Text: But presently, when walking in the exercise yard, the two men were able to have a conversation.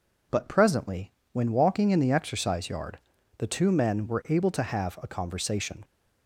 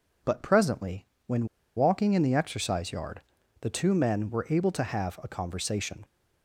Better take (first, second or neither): first